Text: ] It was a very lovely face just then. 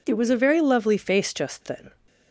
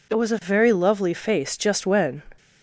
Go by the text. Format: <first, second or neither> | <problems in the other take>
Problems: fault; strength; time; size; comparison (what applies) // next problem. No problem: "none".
first | says "when" for "then"; at 1.8 s